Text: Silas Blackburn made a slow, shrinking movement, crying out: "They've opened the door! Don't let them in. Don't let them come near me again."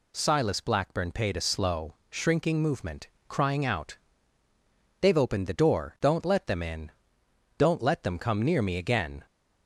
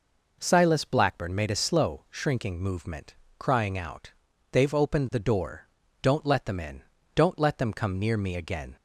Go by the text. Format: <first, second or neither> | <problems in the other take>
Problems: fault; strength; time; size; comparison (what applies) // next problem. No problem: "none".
second | says "paid" for "made"; at 1.1 s